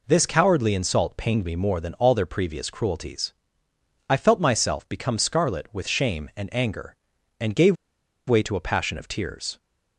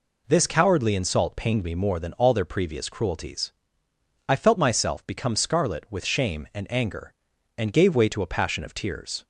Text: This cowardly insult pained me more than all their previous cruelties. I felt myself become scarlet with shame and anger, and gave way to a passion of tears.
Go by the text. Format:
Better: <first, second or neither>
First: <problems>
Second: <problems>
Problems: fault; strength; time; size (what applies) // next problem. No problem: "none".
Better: second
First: pauses between "gave" and "way"; noticeable; at 7.7 s; 0.53 s long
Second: none